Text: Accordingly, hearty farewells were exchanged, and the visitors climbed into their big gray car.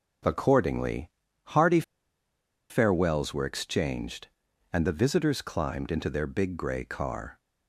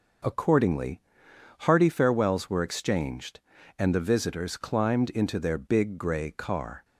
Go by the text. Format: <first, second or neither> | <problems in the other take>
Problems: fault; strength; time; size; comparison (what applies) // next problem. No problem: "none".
second | starts louder than the rest; until 1.6 s; 7 dB // pauses between "hearty" and "farewells"; noticeable; at 1.8 s; 0.88 s long